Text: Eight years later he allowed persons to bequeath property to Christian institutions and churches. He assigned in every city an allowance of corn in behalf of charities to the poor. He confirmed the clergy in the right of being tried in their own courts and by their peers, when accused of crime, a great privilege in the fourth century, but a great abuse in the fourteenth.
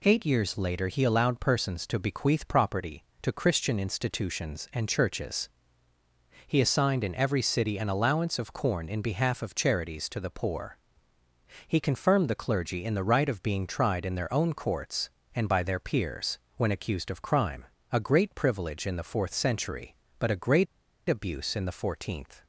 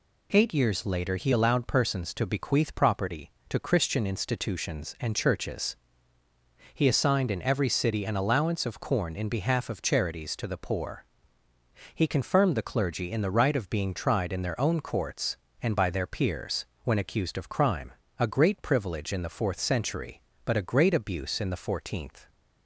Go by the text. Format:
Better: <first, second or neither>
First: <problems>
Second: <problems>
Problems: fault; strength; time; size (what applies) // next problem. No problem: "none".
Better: second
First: pauses between "great" and "abuse"; at 20.6 s; 0.42 s long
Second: none